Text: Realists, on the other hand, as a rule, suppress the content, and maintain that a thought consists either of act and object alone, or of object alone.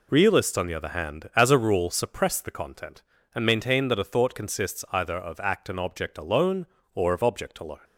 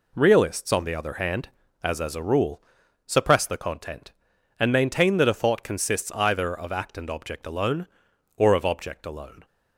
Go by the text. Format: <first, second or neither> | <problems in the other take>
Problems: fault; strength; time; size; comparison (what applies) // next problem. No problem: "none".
first | says "as" twice; at 1.9 s